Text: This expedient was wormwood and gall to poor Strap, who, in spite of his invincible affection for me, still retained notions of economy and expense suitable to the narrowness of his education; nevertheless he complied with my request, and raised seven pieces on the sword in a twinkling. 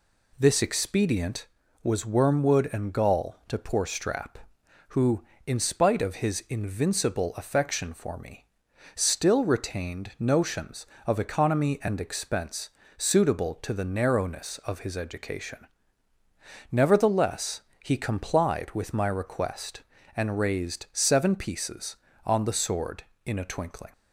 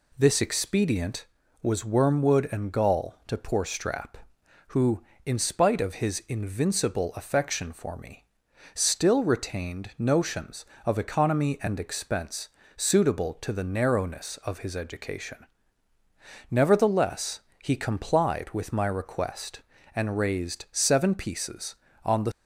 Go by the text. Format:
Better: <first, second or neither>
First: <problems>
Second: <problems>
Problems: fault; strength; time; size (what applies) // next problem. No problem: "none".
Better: first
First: pauses between "expense" and "suitable"; slight; at 12.6 s; 0.28 s long // pauses between "nevertheless" and "he"; slight; at 17.5 s; 0.24 s long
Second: pauses between "expense" and "suitable"; slight; at 12.4 s; 0.28 s long // pauses between "nevertheless" and "he"; slight; at 17.3 s; 0.24 s long // stops before "sword in a twinkling"; at 22.3 s